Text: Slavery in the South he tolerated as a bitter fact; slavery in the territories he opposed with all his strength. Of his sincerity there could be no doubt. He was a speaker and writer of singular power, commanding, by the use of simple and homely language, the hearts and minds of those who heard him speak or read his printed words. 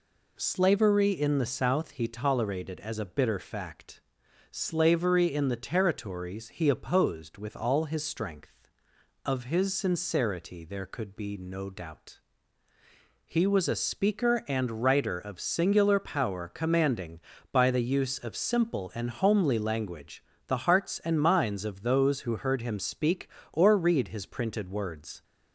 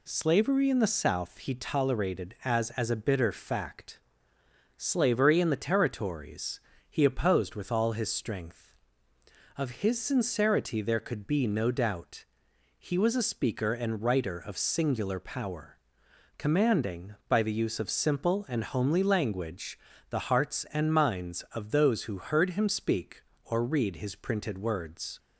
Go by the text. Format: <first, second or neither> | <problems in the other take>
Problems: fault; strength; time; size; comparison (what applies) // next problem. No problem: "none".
first | says "as" twice; at 2.7 s // pauses between "territories" and "he"; slight; at 6.6 s; 0.28 s long